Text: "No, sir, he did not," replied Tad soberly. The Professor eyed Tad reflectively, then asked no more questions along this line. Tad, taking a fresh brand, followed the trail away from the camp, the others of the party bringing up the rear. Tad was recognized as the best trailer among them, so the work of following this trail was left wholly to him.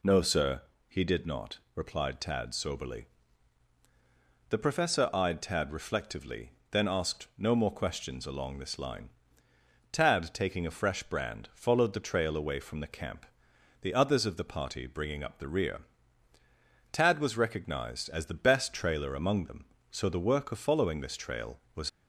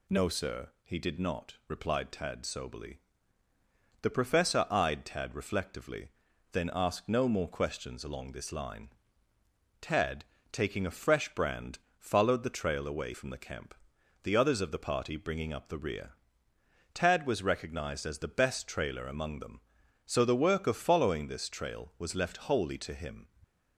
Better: second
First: stops before "left wholly to him"; at 21.8 s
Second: none

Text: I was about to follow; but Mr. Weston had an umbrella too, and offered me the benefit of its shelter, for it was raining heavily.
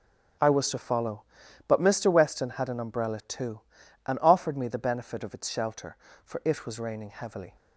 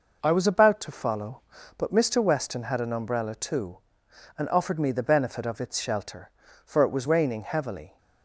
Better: second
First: starts louder than the rest; strong; until 1.8 s; 8.5 dB // skips "about"; at 0.7 s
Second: none

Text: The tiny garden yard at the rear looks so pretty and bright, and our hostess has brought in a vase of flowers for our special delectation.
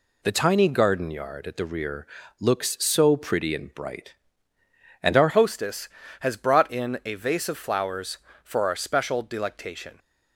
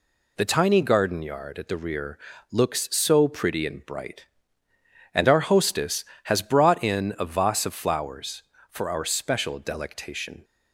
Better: second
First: pauses between "rear" and "looks"; slight; at 2.0 s; 0.34 s long // changes voice at "hostess"; from 5.2 s on; 4.7 s long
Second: pauses between "rear" and "looks"; slight; at 2.1 s; 0.34 s long

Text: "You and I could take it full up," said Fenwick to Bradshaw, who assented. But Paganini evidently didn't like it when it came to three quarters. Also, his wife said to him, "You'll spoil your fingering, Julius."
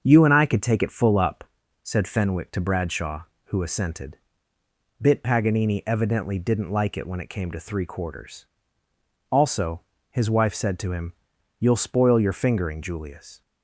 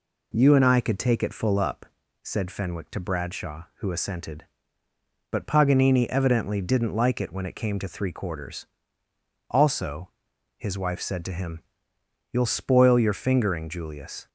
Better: second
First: starts louder than the rest; until 1.0 s; 6.5 dB // says "Bit" for "But"; at 4.9 s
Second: none

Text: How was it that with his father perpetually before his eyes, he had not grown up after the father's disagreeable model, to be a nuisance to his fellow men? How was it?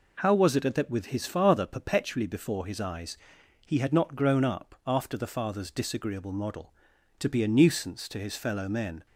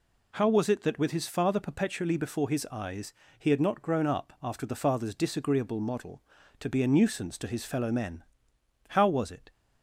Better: second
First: stops before "How was it"; at 9.0 s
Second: none

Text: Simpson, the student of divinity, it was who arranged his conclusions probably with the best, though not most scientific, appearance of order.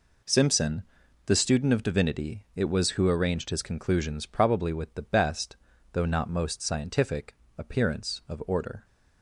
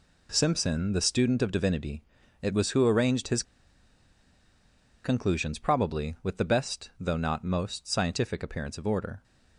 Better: first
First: none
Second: pauses between "his" and "conclusions"; strong; at 3.4 s; 1.6 s long

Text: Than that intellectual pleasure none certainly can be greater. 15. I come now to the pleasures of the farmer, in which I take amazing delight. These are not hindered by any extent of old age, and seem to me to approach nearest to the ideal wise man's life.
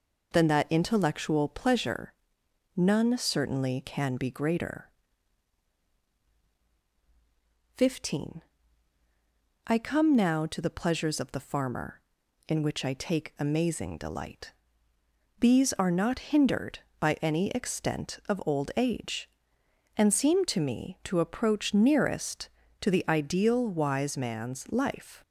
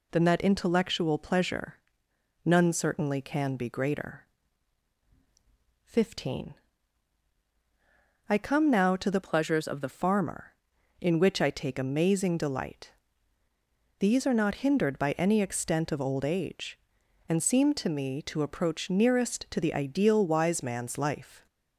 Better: first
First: pauses between "pleasure" and "none"; noticeable; at 2.1 s; 0.64 s long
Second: pauses between "pleasure" and "none"; noticeable; at 1.7 s; 0.70 s long // changes voice from "pleasures" to "the"; from 9.2 to 9.8 s; 0.6 s long

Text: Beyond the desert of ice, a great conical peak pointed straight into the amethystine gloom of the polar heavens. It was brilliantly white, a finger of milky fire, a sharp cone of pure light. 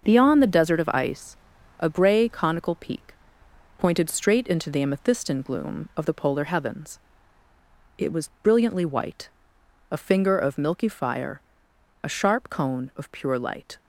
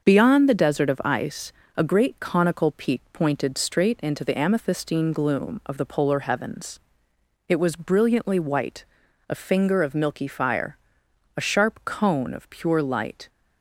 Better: second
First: starts louder than the rest; until 1.0 s; 6.5 dB // says "grey" for "great"; at 1.8 s // pauses between "peak" and "pointed"; noticeable; at 3.1 s; 0.64 s long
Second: starts louder than the rest; until 1.0 s; 6.5 dB

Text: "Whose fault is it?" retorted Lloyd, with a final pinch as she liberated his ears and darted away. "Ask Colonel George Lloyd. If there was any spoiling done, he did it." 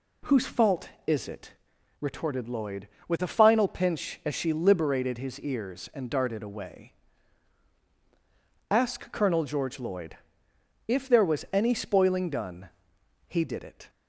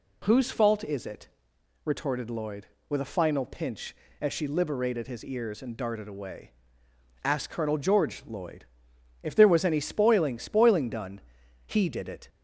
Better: first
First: none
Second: says "spoiling" twice; at 10.3 s

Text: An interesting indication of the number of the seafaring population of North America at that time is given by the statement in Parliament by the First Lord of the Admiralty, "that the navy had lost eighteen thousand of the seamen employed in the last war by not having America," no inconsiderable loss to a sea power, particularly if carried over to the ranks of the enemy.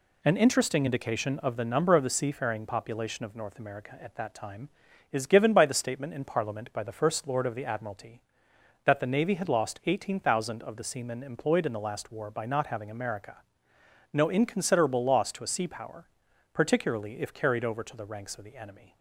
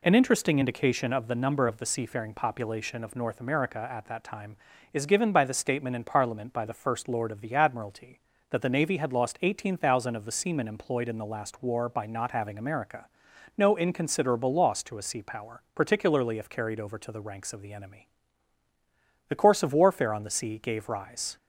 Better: first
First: none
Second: goes on to say "The course of warfare on the sea gave rise"; strong; from 19.2 s on; 2.0 s long

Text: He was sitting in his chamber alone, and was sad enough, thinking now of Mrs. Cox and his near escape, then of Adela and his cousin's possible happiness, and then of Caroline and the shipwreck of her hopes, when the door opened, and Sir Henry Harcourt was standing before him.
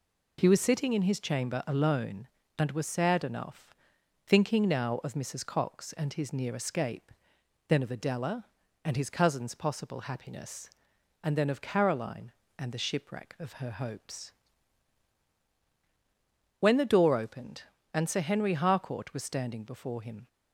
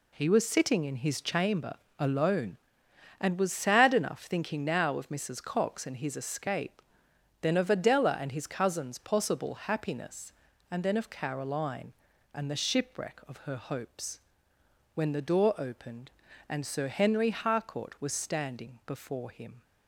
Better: first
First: none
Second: pauses between "chamber" and "alone"; slight; at 1.7 s; 0.24 s long // skips "near"; at 6.1 s

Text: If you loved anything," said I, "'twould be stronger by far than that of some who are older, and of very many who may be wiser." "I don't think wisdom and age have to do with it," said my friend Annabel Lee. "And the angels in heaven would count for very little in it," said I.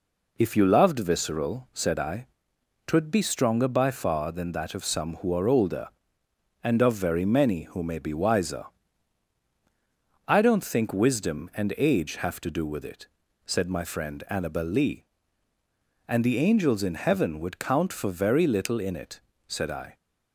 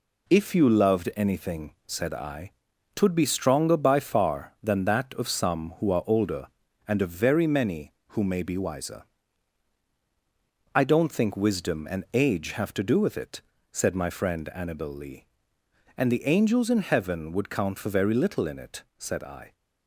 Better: second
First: says "visceral" for "anything"; at 0.9 s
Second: none

